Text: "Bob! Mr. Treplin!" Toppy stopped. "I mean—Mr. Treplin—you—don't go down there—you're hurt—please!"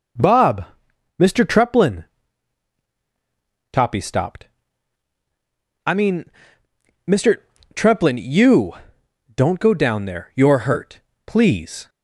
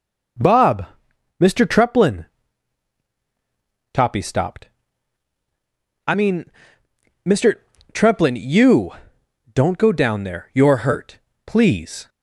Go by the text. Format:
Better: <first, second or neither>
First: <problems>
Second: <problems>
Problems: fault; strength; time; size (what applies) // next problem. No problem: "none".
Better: neither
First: none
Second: none